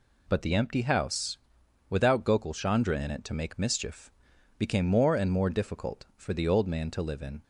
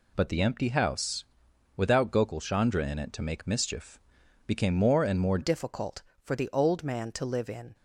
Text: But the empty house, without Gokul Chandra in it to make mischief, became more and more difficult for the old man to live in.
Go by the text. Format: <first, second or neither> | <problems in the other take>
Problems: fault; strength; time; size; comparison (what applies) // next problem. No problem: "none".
first | changes voice at "difficult"; from 5.4 s on; 2.3 s long